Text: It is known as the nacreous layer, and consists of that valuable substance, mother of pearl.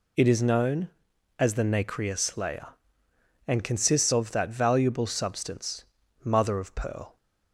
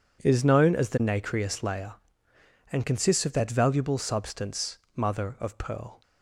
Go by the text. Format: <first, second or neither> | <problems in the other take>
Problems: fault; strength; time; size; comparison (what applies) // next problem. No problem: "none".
neither | none